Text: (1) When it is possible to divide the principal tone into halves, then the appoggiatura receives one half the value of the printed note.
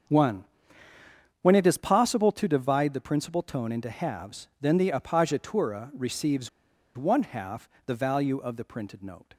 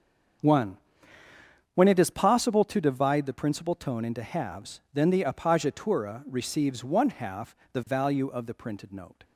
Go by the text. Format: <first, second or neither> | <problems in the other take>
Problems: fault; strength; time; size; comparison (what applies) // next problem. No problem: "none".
second | starts louder than the rest; strong; until 2.0 s; 7.5 dB; strong in the second // pauses between "receives" and "one"; noticeable; at 6.4 s; 0.47 s long // pauses between "half" and "the"; slight; at 7.6 s; 0.18 s long; slight in the second